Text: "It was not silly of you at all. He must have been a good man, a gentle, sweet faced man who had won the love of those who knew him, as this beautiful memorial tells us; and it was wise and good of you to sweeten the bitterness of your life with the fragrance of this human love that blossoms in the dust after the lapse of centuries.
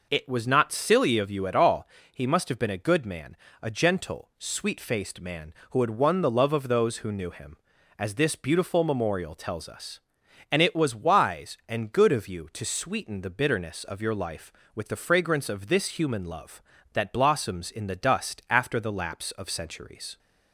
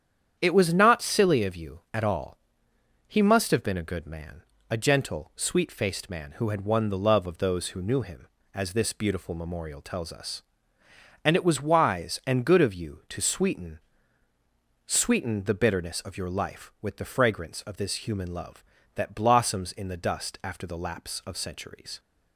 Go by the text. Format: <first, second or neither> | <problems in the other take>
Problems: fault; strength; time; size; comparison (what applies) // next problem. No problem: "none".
first | starts louder than the rest; strong; until 1.4 s; 9 dB // says "sweeten" twice; at 14.8 s